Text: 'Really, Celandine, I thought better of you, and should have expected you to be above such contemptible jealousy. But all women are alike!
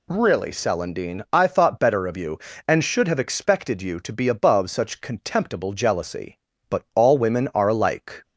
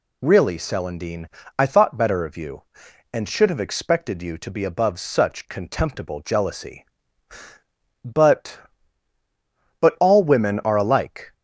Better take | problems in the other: first | says "But" twice; at 9.7 s

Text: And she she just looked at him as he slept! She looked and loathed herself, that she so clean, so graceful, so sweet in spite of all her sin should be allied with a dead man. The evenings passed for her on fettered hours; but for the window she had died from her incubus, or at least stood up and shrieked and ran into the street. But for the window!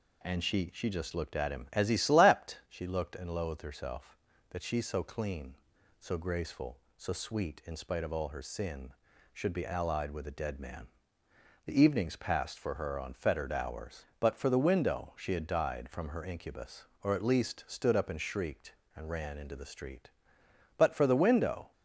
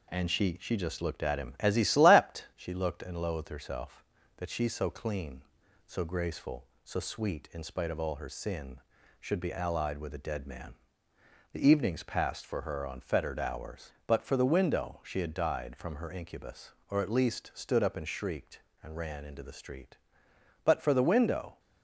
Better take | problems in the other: first | gets quieter; slight; throughout; 2.5 dB

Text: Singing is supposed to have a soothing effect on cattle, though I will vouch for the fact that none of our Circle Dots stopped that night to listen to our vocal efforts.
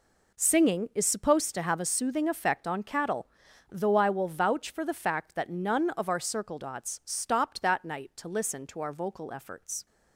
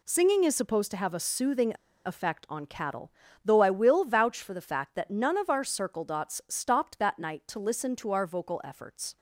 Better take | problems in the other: first | pauses between "soothing" and "effect"; slight; at 1.7 s; 0.33 s long

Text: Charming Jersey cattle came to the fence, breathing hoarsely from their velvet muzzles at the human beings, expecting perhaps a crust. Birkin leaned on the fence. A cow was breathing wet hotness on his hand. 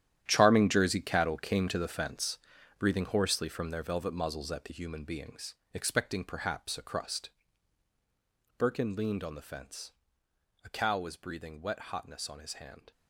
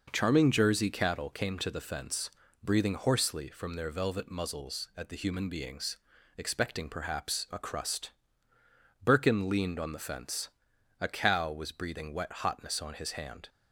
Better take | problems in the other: second | gets quieter; strong; throughout; 13.5 dB

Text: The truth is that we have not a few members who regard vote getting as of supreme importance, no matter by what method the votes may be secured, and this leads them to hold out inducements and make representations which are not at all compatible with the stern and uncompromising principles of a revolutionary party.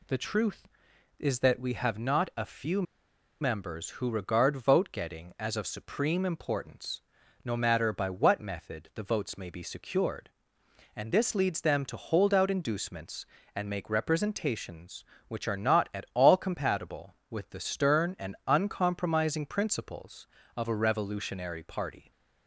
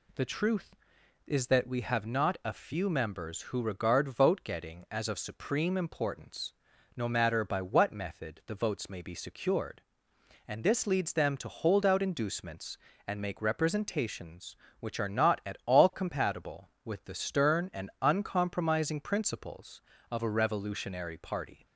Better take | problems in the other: second | pauses between "few" and "members"; noticeable; at 2.8 s; 0.58 s long

